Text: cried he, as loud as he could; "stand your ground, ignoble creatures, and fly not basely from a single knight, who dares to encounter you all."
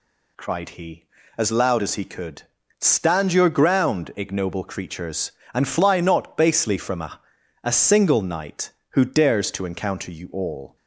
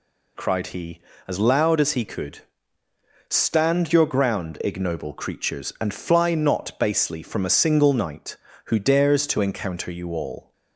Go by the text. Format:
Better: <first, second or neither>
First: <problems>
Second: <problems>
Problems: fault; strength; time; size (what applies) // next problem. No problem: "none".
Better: second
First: says "a" twice; at 7.6 s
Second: none